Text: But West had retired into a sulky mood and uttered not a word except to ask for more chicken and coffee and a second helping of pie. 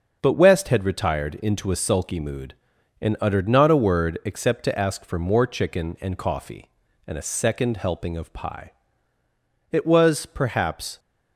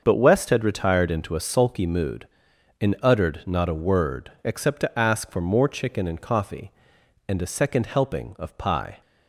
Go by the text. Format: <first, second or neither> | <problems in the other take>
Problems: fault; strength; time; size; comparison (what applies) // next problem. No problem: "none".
second | starts louder than the rest; until 1.2 s; 6 dB; also in the second // goes on to say "It was perhaps"; noticeable; from 9.7 s on; 1.2 s long